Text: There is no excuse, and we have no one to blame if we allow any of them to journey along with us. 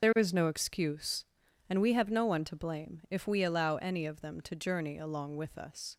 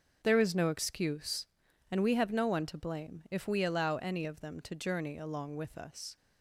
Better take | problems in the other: second | loses the start of "There"; at 0.0 s; 35 ms // starts louder than the rest; until 1.0 s; 6.5 dB; also in the second

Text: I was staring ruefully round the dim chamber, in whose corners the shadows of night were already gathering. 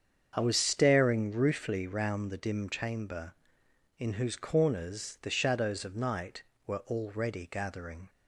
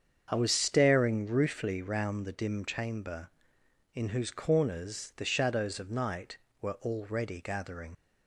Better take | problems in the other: first | starts louder than the rest; until 1.3 s; 7 dB; strong in the first // leaves "gathering" unfinished; at 7.9 s; 70 ms

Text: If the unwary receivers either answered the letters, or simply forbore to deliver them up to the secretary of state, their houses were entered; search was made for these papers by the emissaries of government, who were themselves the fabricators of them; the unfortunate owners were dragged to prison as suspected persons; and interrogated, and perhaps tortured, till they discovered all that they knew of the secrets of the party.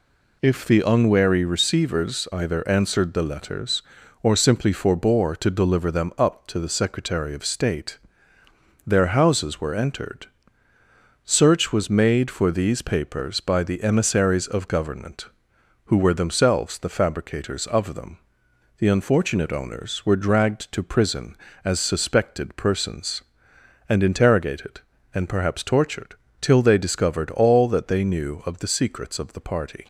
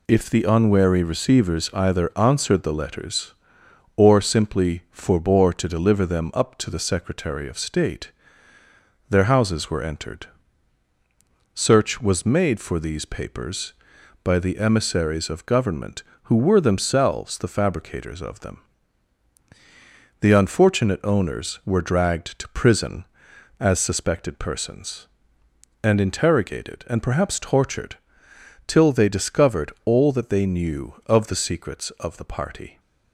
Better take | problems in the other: neither | none

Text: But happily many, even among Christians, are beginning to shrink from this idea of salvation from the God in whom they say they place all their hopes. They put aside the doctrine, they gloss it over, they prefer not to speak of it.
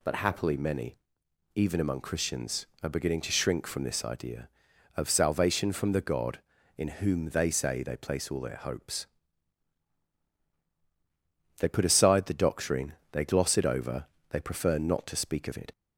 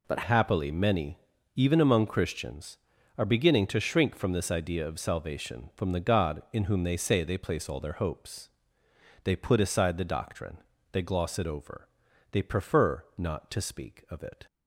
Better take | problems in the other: first | changes voice at "happily"; from 0.2 s on; 14.2 s long

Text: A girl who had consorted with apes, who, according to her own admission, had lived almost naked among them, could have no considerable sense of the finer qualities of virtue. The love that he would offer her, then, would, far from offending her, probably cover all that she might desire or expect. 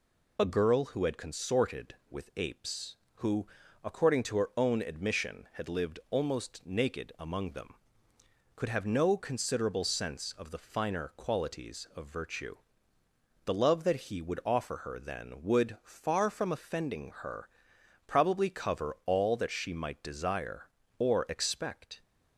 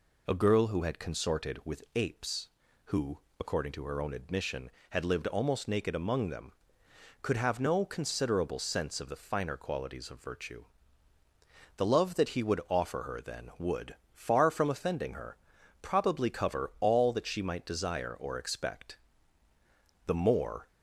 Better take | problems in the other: first | goes on to say "The more"; noticeable; from 20.0 s on; 0.62 s long

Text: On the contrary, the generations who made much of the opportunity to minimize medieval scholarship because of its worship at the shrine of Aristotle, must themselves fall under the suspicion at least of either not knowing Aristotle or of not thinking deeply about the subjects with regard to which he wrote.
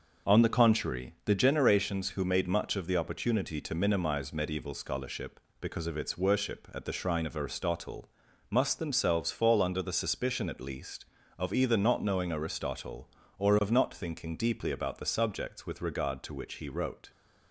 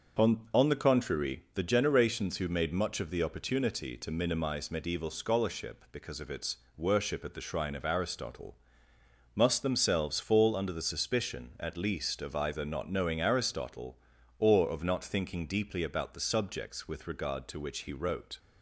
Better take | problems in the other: first | says "On" twice; at 0.5 s // pauses between "its" and "worship"; slight; at 6.5 s; 0.18 s long

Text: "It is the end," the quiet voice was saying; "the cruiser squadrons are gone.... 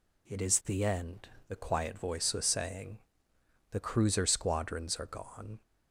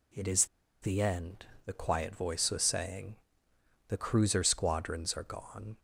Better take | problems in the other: first | pauses between "is" and "the"; slight; at 0.4 s; 0.35 s long

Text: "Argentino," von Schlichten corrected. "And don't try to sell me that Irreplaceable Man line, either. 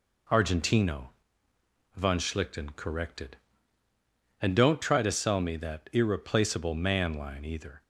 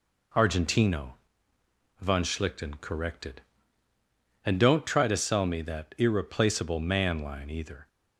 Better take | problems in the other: neither | none

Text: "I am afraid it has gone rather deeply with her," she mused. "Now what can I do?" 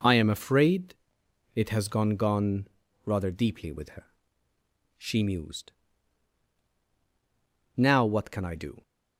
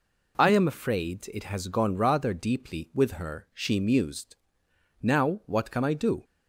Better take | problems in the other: second | pauses between "afraid" and "it"; noticeable; at 0.9 s; 0.58 s long // says "gone" twice; at 2.1 s

